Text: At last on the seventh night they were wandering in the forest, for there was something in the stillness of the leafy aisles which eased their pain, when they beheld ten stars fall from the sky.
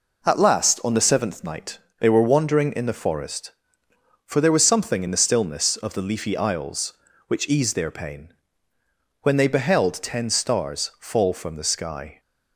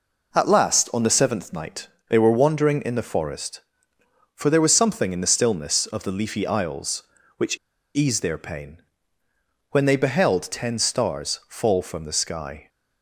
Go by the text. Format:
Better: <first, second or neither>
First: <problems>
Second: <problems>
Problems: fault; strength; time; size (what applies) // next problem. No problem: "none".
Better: first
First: pauses between "night" and "they"; slight; at 1.7 s; 0.18 s long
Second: pauses between "night" and "they"; slight; at 1.8 s; 0.18 s long // pauses between "which" and "eased"; at 7.5 s; 0.37 s long